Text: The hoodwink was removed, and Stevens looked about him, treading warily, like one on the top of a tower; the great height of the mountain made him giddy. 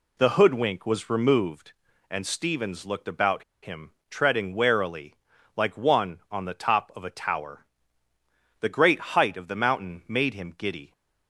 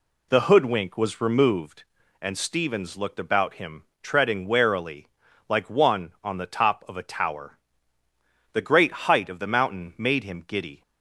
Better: second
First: pauses between "about" and "him"; slight; at 3.4 s; 0.19 s long // pauses between "great" and "height"; slight; at 8.9 s; 0.16 s long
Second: pauses between "great" and "height"; slight; at 8.9 s; 0.16 s long

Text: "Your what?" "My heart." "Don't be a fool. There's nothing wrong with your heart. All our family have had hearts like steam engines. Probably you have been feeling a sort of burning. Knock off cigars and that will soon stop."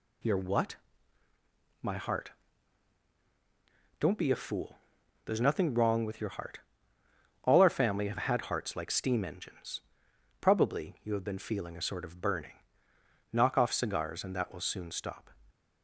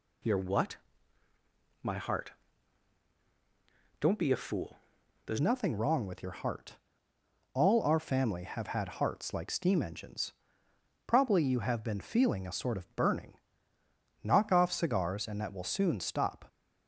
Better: first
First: none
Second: changes voice at "nothing"; from 5.4 s on; 11.0 s long

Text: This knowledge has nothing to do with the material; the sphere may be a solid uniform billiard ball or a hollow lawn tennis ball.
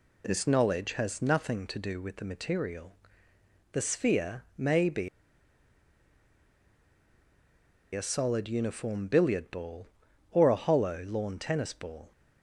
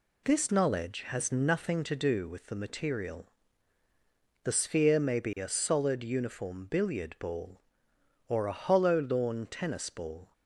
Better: second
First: pauses between "sphere" and "may"; slight; at 4.4 s; 0.16 s long // pauses between "be" and "a"; strong; at 5.0 s; 2.8 s long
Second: none

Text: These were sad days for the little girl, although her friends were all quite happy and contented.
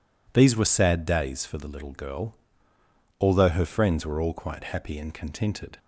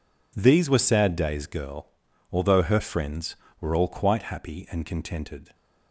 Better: first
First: none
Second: skips "for the little"; at 1.4 s

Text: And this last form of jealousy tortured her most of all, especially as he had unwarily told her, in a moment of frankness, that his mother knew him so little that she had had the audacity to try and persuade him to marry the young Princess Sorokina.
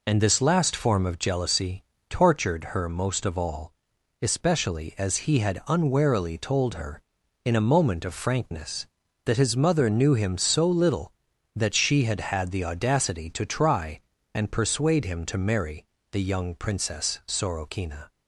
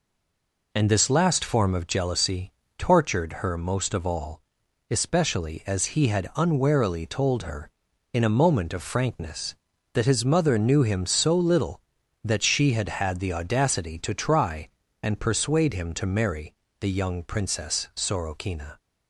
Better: first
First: pauses between "jealousy" and "tortured"; slight; at 1.8 s; 0.26 s long // pauses between "marry" and "the"; slight; at 15.8 s; 0.26 s long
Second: stays silent before the first word; slight; until 0.7 s; 0.7 s long // pauses between "jealousy" and "tortured"; slight; at 2.5 s; 0.26 s long // pauses between "marry" and "the"; slight; at 16.5 s; 0.26 s long

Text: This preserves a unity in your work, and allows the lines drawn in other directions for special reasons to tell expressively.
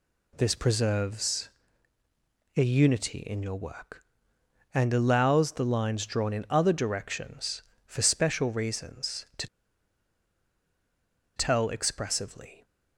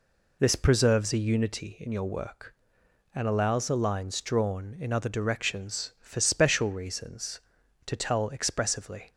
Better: second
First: pauses between "preserves" and "a"; at 1.4 s; 1.0 s long // pauses between "to" and "tell"; strong; at 9.4 s; 1.9 s long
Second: none

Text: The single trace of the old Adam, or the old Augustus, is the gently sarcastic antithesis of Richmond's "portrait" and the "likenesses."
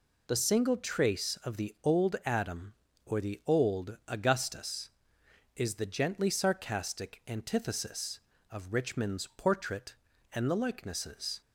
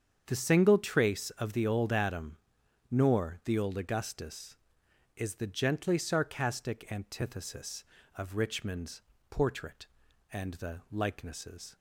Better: first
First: none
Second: starts louder than the rest; strong; until 1.2 s; 7.5 dB // says "nor" for "or"; at 2.8 s // pauses between "Richmond's" and "portrait"; slight; at 9.0 s; 0.30 s long

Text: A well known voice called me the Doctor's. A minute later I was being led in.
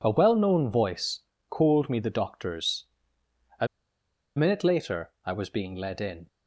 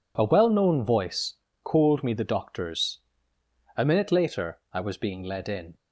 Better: second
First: pauses between "voice" and "called"; slight; at 1.2 s; 0.28 s long // pauses between "A" and "minute"; noticeable; at 3.6 s; 0.70 s long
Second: pauses between "voice" and "called"; slight; at 1.3 s; 0.28 s long

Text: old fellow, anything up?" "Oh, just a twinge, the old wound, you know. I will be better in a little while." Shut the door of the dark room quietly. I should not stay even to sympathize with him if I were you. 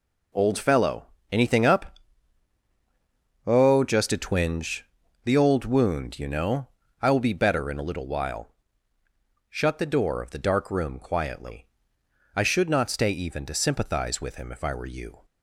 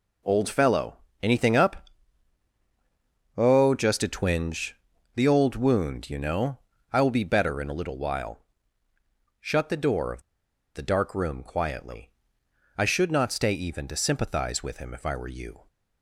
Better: first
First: none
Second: pauses between "of" and "the"; noticeable; at 10.2 s; 0.54 s long

